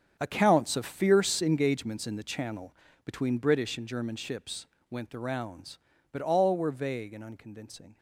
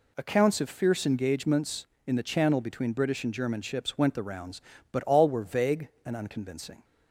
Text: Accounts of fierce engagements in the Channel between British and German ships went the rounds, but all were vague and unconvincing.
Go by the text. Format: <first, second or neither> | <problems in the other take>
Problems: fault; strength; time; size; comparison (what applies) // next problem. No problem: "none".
second | gets quieter; strong; throughout; 13.5 dB // pauses between "Channel" and "between"; slight; at 2.7 s; 0.30 s long // pauses between "ships" and "went"; slight; at 4.6 s; 0.24 s long